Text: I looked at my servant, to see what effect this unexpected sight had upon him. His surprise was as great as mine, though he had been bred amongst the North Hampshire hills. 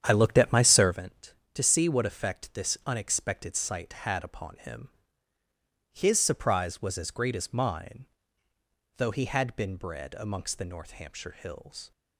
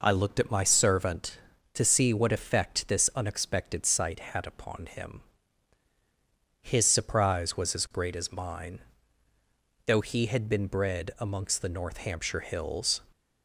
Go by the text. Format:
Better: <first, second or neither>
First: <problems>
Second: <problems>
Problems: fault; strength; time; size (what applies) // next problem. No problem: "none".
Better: second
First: starts louder than the rest; strong; until 1.0 s; 9 dB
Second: none